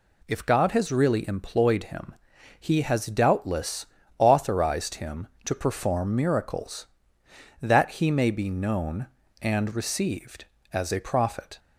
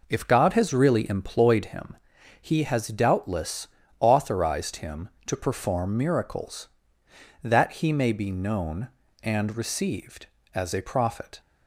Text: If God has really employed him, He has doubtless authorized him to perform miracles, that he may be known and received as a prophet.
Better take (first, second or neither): first